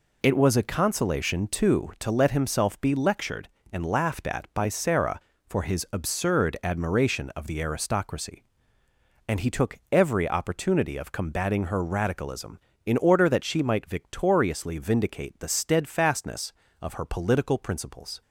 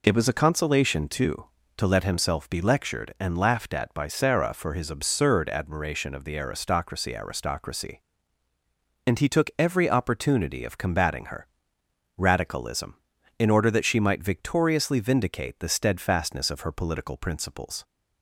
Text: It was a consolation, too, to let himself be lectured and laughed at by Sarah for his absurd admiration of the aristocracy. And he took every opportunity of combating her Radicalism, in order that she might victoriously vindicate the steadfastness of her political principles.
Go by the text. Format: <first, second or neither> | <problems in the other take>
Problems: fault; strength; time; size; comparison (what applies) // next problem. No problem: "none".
first | says "aristocracy" twice; at 7.1 s // pauses between "her" and "Radicalism"; noticeable; at 11.4 s; 0.70 s long